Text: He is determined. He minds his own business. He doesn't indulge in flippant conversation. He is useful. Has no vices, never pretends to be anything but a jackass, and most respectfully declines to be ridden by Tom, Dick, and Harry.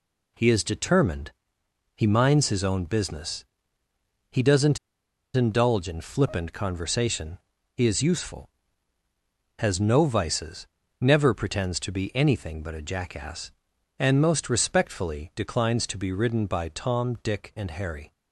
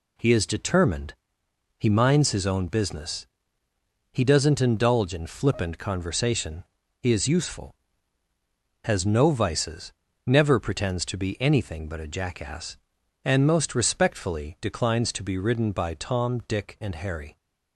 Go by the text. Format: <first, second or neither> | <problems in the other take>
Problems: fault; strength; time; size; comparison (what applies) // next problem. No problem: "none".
second | pauses between "doesn't" and "indulge"; noticeable; at 4.7 s; 0.57 s long